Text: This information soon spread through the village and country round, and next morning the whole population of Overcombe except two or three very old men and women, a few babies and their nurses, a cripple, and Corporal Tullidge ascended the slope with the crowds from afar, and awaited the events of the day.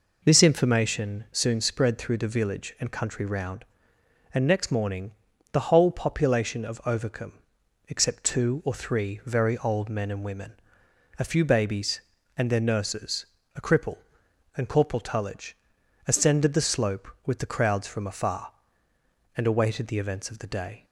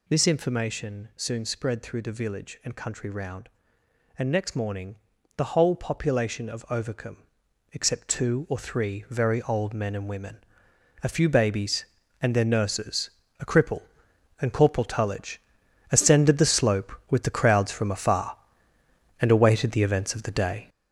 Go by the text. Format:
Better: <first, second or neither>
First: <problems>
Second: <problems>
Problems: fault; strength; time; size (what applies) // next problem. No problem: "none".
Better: first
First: pauses between "morning" and "the"; at 5.1 s; 0.40 s long // pauses between "Overcombe" and "except"; noticeable; at 7.3 s; 0.56 s long // pauses between "Tullidge" and "ascended"; noticeable; at 15.5 s; 0.52 s long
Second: gets louder; strong; throughout; 8 dB // pauses between "morning" and "the"; at 4.9 s; 0.40 s long // pauses between "Overcombe" and "except"; noticeable; at 7.1 s; 0.56 s long // pauses between "Tullidge" and "ascended"; noticeable; at 15.3 s; 0.52 s long